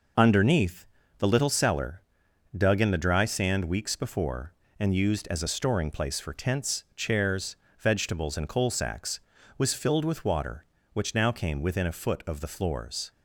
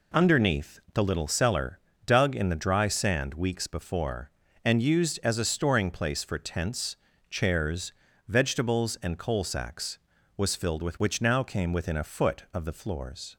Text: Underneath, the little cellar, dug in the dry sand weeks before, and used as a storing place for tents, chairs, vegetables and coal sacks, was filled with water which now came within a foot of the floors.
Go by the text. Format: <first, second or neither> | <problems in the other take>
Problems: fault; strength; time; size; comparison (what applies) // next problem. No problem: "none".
first | skips "water"; at 10.9 s